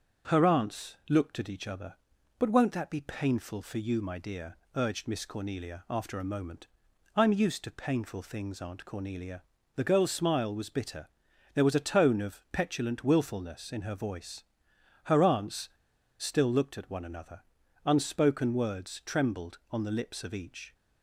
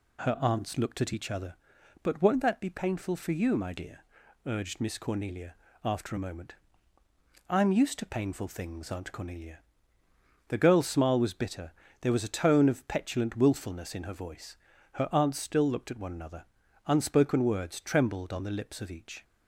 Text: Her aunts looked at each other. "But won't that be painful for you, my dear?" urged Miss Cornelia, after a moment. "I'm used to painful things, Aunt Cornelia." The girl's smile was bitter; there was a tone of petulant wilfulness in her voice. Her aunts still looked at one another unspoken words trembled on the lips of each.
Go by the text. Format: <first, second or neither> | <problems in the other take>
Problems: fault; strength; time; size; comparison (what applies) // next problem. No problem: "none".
second | starts louder than the rest; strong; until 1.3 s; 7 dB // pauses between "aunts" and "still"; noticeable; at 15.6 s; 0.49 s long // pauses between "another" and "unspoken"; at 17.4 s; 0.42 s long; also in the second